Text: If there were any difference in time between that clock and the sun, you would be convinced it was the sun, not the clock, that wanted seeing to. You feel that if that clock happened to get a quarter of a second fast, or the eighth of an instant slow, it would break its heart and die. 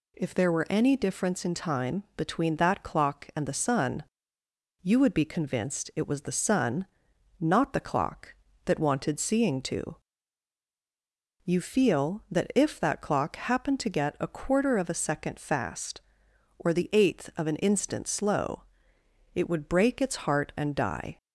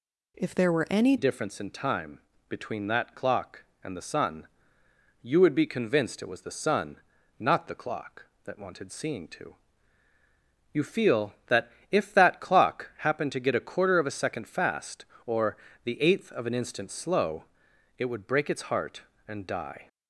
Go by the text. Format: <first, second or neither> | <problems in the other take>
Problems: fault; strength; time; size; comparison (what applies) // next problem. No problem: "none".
first | changes voice at "difference"; from 1.1 s on; 18.7 s long // pauses between "time" and "between"; slight; at 2.1 s; 0.28 s long // pauses between "that" and "if"; slight; at 11.6 s; 0.20 s long // pauses between "or" and "the"; slight; at 15.5 s; 0.28 s long